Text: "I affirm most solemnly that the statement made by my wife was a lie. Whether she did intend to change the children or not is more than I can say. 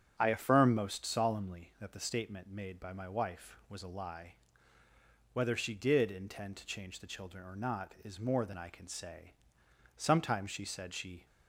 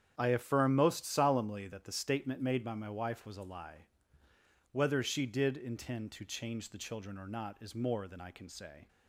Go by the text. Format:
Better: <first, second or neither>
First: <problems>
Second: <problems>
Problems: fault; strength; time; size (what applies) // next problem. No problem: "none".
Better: second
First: starts louder than the rest; strong; until 1.1 s; 7.5 dB // goes on to say "Sometimes she said she"; noticeable; from 9.9 s on; 1.2 s long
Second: starts louder than the rest; strong; until 1.1 s; 8.5 dB